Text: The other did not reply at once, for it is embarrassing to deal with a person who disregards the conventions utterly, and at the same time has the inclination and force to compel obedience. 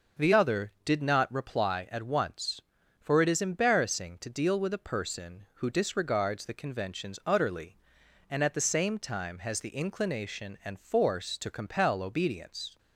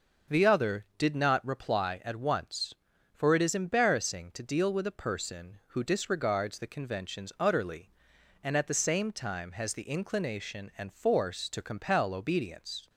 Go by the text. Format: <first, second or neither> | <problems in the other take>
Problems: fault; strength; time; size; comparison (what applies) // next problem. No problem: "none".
neither | starts louder than the rest; the same in both